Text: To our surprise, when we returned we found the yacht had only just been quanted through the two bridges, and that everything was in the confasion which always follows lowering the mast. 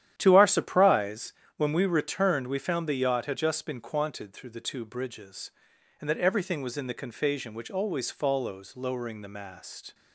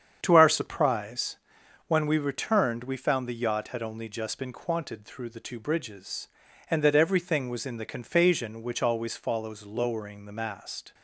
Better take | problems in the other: second | starts louder than the rest; strong; until 1.1 s; 10.5 dB; strong in the second // skips "only"; at 3.3 s

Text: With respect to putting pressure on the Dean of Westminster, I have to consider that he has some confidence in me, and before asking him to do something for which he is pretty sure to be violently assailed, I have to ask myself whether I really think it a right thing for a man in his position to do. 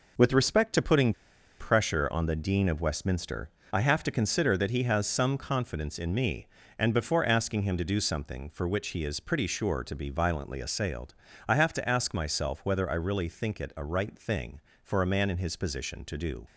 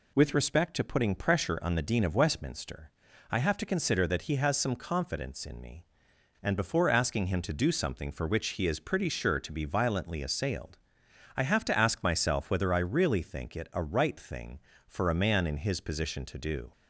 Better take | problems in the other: second | pauses between "putting" and "pressure"; noticeable; at 1.1 s; 0.48 s long

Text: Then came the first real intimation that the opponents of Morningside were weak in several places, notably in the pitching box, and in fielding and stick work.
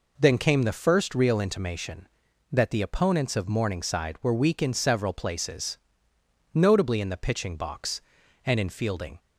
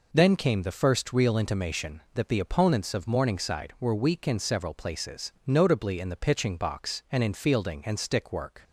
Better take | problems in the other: second | stops before "and stick work"; at 9.1 s

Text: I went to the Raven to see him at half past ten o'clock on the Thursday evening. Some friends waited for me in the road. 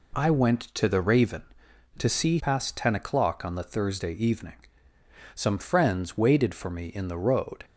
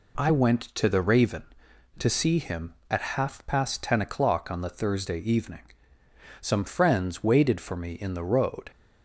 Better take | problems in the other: second | skips "him at half"; at 2.3 s

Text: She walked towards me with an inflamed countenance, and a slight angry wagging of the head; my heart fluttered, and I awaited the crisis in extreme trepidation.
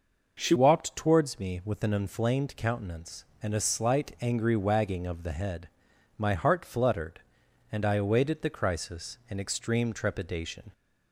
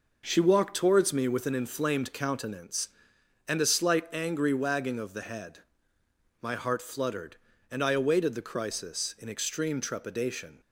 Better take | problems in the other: second | changes voice at "walked"; from 0.5 s on; 10.2 s long

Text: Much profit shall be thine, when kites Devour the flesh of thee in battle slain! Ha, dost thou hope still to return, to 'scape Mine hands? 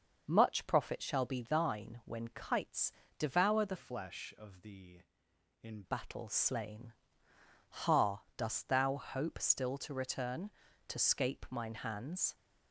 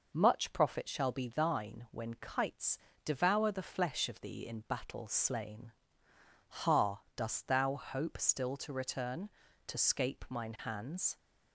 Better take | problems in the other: second | pauses between "kites" and "Devour"; slight; at 2.9 s; 0.26 s long; slight in the second // changes voice from "flesh" to "in"; from 3.7 to 5.8 s; 2.1 s long

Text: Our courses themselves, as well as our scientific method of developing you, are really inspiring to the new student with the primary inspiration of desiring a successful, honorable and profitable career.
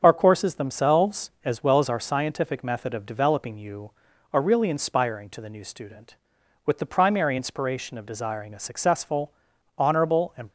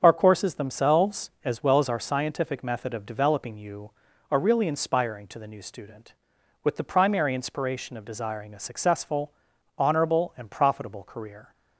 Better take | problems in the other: second | starts louder than the rest; until 1.0 s; 7 dB; strong in the second // stops before "profitable career"; at 10.4 s

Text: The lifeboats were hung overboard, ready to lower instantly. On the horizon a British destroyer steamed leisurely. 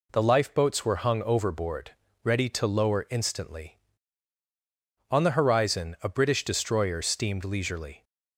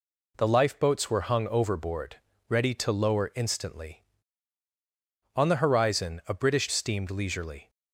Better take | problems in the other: first | skips "destroyer"; at 6.6 s

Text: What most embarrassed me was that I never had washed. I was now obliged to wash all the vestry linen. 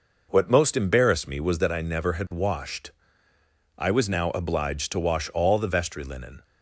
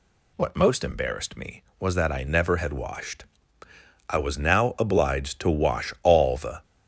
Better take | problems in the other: first | stops before "vestry linen"; at 6.6 s

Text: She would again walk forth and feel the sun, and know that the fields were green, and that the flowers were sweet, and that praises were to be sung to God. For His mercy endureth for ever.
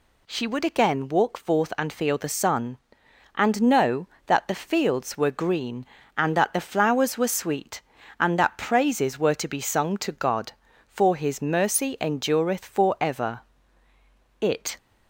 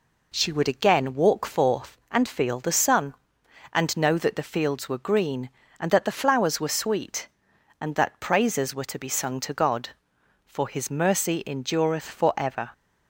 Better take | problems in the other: second | goes on to say "It"; slight; from 14.4 s on; 0.36 s long

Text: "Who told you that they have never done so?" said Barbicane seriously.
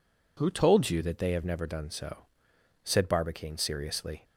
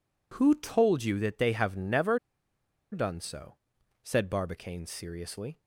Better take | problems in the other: first | pauses between "never" and "done"; noticeable; at 2.1 s; 0.73 s long

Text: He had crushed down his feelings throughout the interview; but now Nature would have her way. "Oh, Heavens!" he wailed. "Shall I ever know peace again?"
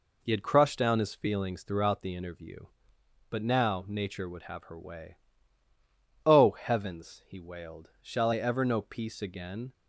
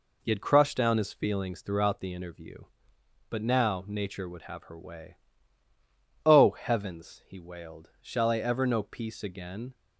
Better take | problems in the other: neither | none

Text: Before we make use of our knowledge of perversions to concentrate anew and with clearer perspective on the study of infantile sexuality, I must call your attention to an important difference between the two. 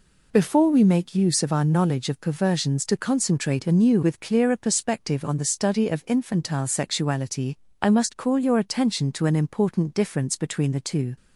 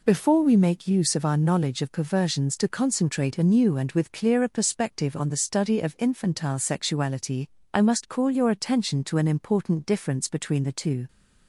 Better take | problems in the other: second | skips "and"; at 4.0 s

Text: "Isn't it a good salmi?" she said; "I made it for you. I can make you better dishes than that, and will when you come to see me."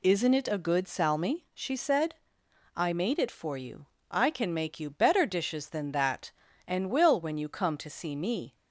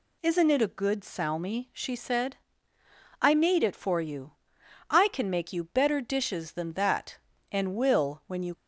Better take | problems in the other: first | stops before "come to see me"; at 8.5 s

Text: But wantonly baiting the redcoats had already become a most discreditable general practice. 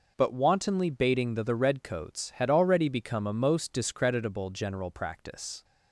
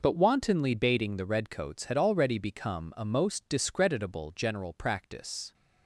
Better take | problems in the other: second | says "the" twice; at 1.4 s

